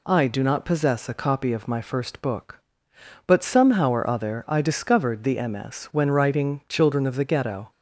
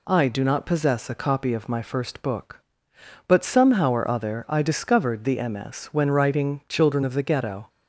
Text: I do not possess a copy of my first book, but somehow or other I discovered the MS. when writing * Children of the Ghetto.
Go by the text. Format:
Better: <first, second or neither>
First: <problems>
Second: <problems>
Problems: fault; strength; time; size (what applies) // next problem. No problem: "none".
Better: neither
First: none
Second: none